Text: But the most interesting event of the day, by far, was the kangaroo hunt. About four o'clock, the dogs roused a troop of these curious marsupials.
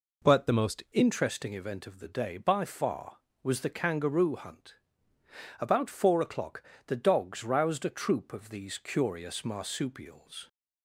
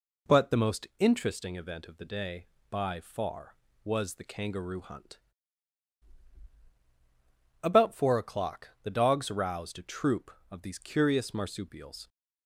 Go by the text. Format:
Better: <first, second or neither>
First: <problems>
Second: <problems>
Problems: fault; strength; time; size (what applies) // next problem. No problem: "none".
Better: second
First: changes voice at "interesting"; from 0.9 s on; 9.5 s long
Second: none